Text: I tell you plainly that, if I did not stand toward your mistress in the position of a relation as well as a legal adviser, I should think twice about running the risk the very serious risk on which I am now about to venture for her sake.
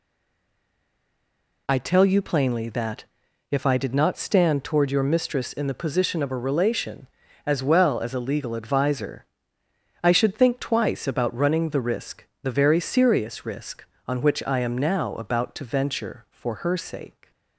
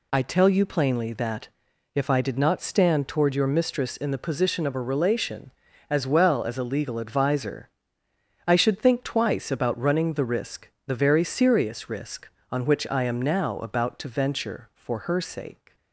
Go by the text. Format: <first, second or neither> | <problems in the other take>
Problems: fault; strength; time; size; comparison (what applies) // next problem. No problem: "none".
second | stays silent before the first word; noticeable; until 1.6 s; 1.6 s long // pauses between "risk" and "the"; slight; at 12.2 s; 0.18 s long; slight in the second